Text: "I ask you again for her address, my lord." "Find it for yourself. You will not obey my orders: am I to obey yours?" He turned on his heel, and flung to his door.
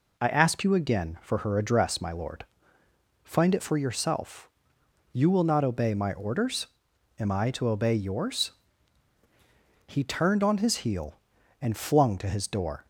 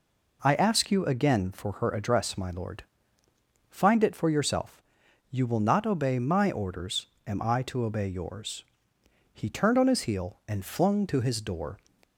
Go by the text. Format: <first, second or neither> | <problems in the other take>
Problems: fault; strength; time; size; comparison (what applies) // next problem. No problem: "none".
neither | none